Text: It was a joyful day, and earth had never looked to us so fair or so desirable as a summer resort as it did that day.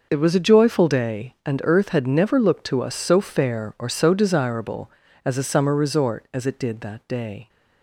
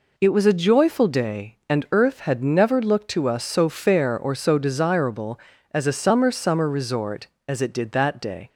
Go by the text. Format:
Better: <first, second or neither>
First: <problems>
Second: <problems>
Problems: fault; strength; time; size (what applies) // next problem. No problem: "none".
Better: first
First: none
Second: says "summer" twice; at 6.3 s